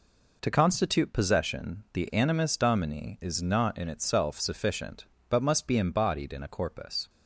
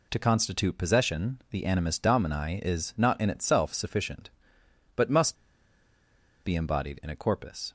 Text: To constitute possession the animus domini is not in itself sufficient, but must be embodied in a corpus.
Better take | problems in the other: first | pauses between "must" and "be"; at 5.3 s; 1.0 s long

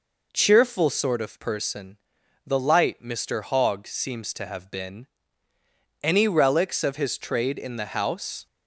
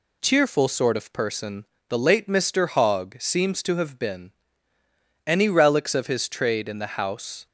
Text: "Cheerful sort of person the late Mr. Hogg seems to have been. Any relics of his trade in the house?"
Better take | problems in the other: second | pauses between "person" and "the"; noticeable; at 1.9 s; 0.48 s long; slight in the second // says "light" for "late"; at 2.5 s

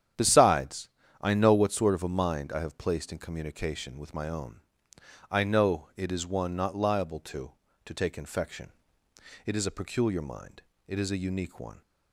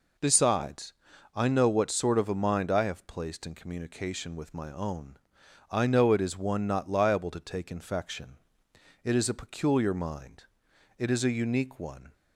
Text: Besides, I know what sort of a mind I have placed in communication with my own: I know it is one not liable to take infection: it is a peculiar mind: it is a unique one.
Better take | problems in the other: second | starts louder than the rest; strong; until 1.4 s; 9.5 dB // says "to" twice; at 7.8 s

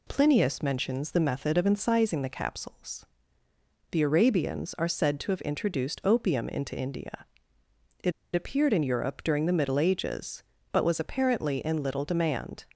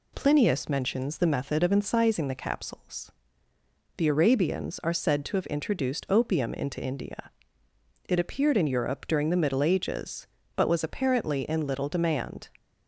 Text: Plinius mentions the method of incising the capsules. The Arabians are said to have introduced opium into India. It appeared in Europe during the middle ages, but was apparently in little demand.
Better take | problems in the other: second | pauses between "It" and "appeared"; slight; at 8.1 s; 0.23 s long

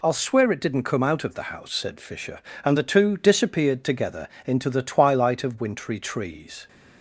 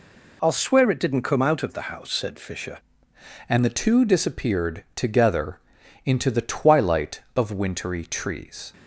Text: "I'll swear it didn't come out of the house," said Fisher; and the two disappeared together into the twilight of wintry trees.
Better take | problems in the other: first | changes voice at "and"; from 3.4 s on; 5.3 s long // pauses between "together" and "into"; at 5.6 s; 0.44 s long; slight in the first

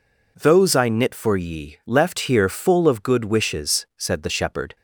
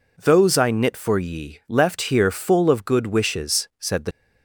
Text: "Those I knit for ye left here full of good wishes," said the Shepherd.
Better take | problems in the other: first | stops before "Shepherd"; at 4.1 s

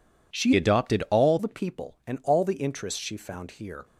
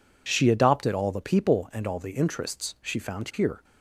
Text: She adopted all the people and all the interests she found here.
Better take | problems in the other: second | changes voice from "adopted" to "all"; from 0.5 to 1.3 s; 0.8 s long

